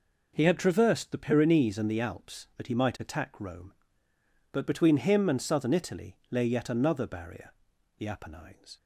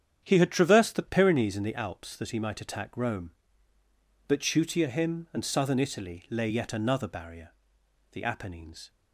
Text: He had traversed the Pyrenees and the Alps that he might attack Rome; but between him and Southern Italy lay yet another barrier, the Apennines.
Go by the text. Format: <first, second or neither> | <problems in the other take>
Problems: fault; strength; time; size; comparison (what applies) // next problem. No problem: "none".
first | starts louder than the rest; strong; until 1.2 s; 8.5 dB // says "chutia" for "between"; at 4.3 s